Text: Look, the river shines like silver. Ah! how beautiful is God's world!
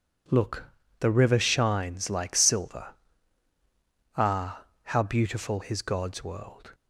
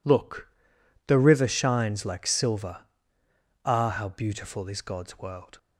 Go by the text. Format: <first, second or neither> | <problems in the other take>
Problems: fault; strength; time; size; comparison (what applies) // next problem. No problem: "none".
second | says "his" for "is"; at 5.6 s